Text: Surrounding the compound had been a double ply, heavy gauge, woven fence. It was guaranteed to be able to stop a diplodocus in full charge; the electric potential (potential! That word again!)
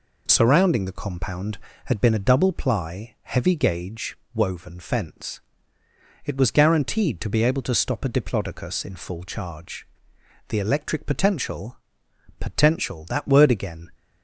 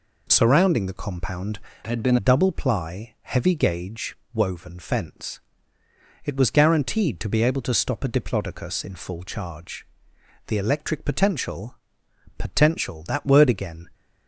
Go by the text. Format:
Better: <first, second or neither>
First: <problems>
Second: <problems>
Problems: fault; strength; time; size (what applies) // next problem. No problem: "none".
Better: first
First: none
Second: changes voice from "had" to "been"; from 1.8 to 2.1 s; 0.3 s long